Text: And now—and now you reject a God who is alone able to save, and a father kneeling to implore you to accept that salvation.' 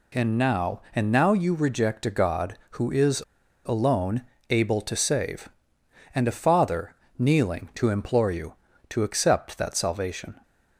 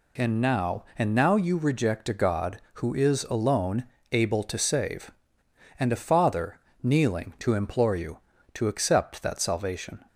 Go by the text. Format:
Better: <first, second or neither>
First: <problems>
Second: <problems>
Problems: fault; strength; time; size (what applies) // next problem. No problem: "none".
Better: second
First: pauses between "is" and "alone"; at 3.2 s; 0.43 s long // pauses between "alone" and "able"; slight; at 4.2 s; 0.28 s long // pauses between "father" and "kneeling"; slight; at 6.9 s; 0.24 s long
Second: pauses between "alone" and "able"; slight; at 3.8 s; 0.28 s long // pauses between "father" and "kneeling"; slight; at 6.5 s; 0.24 s long